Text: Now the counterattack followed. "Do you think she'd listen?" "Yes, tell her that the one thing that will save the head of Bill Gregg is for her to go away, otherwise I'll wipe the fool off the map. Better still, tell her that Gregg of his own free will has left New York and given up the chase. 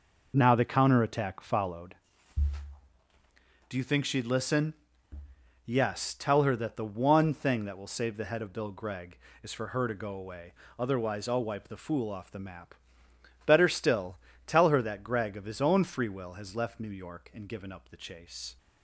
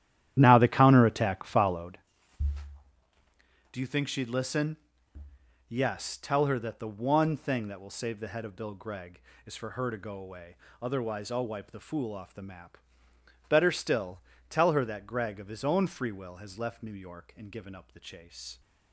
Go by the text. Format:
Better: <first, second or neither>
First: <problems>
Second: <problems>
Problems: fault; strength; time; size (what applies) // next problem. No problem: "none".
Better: first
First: none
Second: starts louder than the rest; strong; until 2.1 s; 12 dB